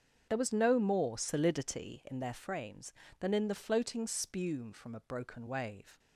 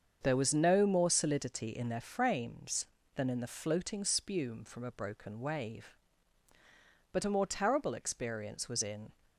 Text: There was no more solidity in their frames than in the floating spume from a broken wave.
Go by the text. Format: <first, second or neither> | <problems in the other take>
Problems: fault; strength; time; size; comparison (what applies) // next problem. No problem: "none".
first | starts louder than the rest; until 1.2 s; 7 dB; strong in the first // goes on to say "But a more terrible experience was in"; strong; from 7.1 s on; 2.0 s long